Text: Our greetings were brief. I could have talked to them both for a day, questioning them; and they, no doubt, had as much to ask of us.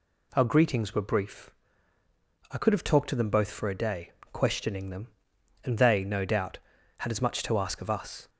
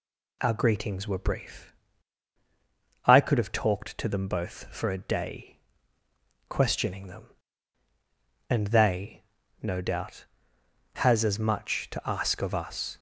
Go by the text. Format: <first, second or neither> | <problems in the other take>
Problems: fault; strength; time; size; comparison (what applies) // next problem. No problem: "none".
first | says "has" for "had"; at 10.9 s